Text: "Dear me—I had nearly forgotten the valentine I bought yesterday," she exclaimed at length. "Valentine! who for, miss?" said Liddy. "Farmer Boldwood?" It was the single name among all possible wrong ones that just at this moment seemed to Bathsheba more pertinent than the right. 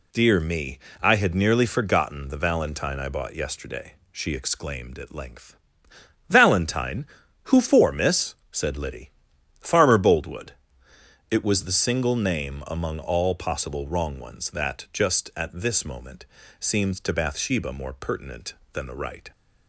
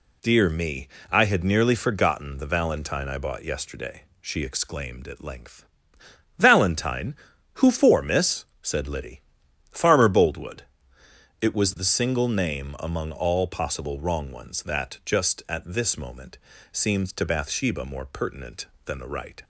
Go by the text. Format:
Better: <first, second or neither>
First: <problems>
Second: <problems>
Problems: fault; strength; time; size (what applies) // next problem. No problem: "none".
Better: neither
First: pauses between "moment" and "seemed"; slight; at 16.2 s; 0.36 s long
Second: pauses between "moment" and "seemed"; slight; at 16.3 s; 0.36 s long